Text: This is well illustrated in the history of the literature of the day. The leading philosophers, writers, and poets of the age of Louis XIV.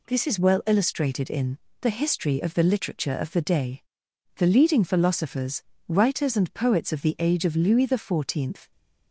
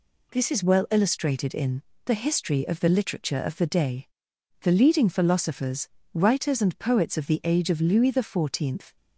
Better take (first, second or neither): neither